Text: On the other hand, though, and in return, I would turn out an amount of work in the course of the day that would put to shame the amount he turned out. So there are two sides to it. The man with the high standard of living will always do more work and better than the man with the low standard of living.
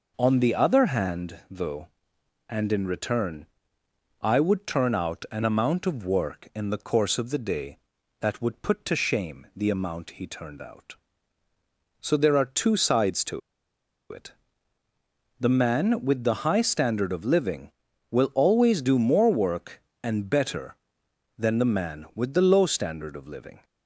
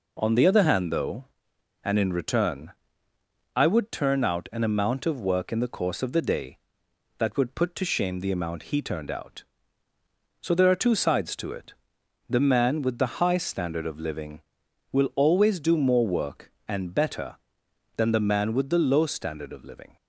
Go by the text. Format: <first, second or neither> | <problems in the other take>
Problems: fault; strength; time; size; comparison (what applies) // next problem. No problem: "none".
second | pauses between "to" and "it"; noticeable; at 13.4 s; 0.71 s long